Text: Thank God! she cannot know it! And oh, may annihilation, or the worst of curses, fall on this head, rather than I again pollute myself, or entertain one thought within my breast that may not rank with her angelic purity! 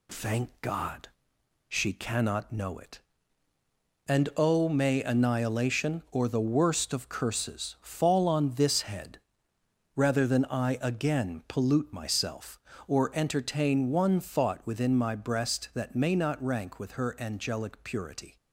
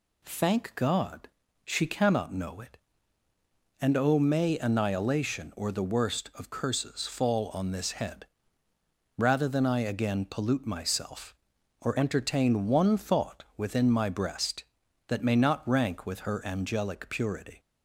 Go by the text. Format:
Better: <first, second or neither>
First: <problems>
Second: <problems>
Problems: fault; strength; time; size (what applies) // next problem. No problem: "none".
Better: neither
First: none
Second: none